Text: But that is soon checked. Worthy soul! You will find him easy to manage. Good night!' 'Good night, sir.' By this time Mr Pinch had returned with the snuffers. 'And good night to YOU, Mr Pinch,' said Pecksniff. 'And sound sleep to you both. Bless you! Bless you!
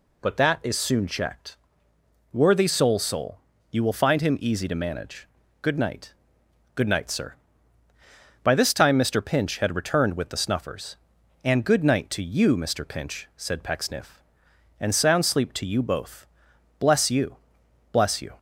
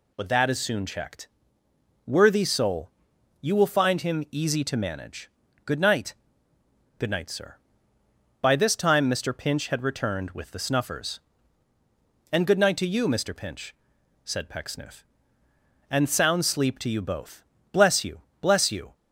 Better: second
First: says "soul" twice; at 2.9 s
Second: none

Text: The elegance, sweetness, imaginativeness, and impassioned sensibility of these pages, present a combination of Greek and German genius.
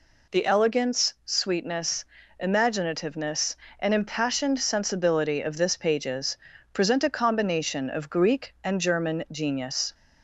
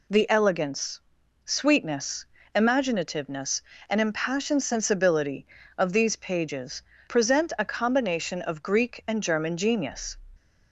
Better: second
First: says "this" for "these"; at 5.5 s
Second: none

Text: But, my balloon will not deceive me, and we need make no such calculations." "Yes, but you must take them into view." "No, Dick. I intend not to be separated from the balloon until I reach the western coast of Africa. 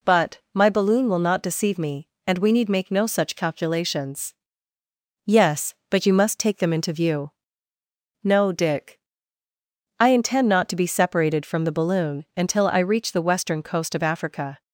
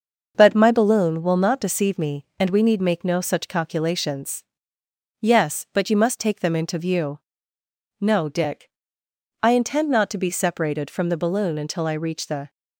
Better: first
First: none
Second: starts louder than the rest; noticeable; until 1.3 s; 6 dB // stops before "western coast of Africa"; at 12.4 s

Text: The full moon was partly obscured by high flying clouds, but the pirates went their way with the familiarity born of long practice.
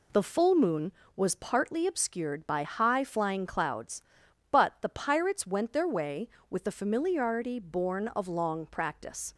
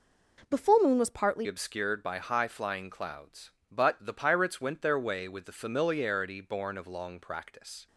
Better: first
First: none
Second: changes voice at "obscured"; from 1.4 s on; 6.4 s long

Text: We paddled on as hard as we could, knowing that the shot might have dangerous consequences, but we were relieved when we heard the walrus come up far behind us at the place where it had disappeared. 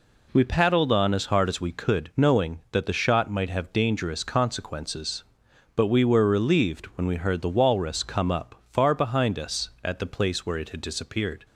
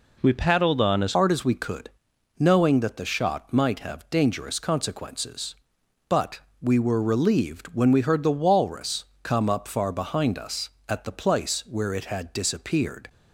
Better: first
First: none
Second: changes voice at "hard"; from 1.1 s on; 11.9 s long // pauses between "but" and "we"; slight; at 6.3 s; 0.22 s long // pauses between "walrus" and "come"; slight; at 9.0 s; 0.20 s long

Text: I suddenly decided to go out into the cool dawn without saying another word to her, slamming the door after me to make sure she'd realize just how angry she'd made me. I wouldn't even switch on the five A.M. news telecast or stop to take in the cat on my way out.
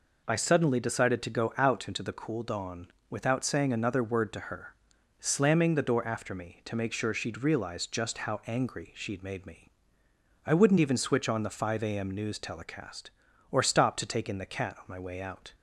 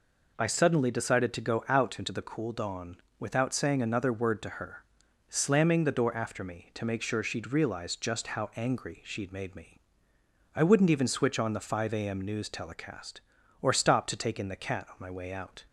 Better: neither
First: pauses between "dawn" and "without"; slight; at 2.8 s; 0.22 s long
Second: pauses between "dawn" and "without"; slight; at 2.9 s; 0.22 s long

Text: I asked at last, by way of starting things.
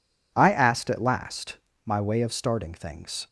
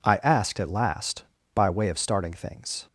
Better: second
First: says "my" for "by"; at 1.8 s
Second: none

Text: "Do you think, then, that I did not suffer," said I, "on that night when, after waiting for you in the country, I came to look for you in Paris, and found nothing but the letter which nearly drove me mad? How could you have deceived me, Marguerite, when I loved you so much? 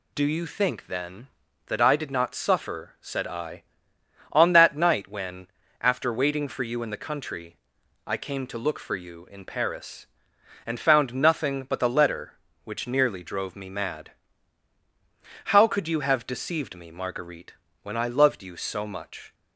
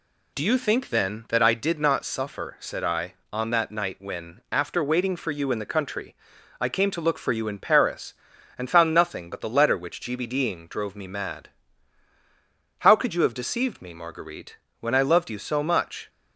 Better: first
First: none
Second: says "gbding" for "nearly"; at 10.0 s

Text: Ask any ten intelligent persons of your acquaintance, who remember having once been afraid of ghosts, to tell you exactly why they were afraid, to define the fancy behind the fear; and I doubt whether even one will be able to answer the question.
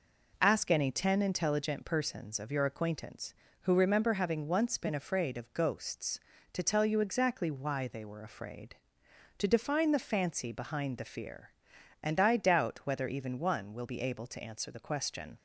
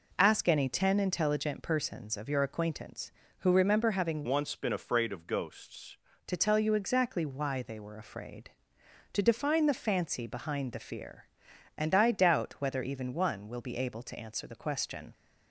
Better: first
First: none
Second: changes voice from "once" to "ghosts"; from 4.2 to 5.9 s; 1.7 s long

